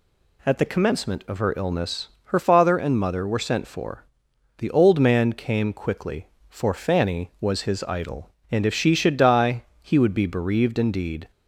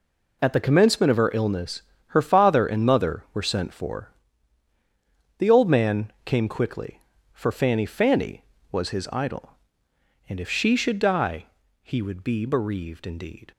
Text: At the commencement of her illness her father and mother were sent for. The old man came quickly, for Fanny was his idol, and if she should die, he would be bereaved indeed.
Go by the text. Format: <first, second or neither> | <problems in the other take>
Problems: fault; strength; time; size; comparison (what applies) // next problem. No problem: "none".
first | pauses between "illness" and "her"; slight; at 1.8 s; 0.26 s long; slight in the first // says "Fanny" twice; at 7.8 s